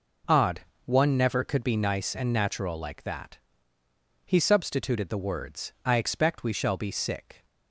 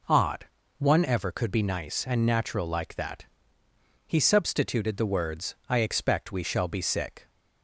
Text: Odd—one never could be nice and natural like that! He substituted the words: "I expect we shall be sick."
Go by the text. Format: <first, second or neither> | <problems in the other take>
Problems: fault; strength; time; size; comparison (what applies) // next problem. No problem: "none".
first | says "ever" for "never"; at 1.0 s